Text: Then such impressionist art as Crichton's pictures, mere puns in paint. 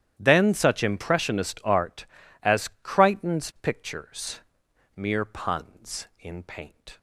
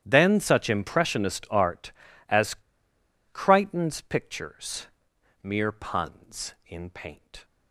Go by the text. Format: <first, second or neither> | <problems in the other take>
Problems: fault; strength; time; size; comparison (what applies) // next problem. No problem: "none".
first | starts louder than the rest; strong; until 1.0 s; 11.5 dB; strong in the first // pauses between "as" and "Crichton's"; noticeable; at 2.5 s; 0.77 s long